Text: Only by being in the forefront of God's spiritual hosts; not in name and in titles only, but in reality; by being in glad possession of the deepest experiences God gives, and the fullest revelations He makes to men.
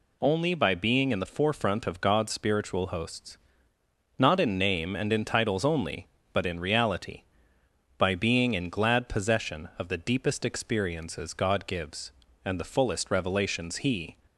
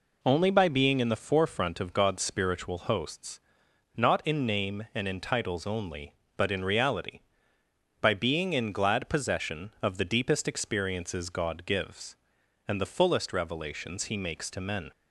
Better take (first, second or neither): second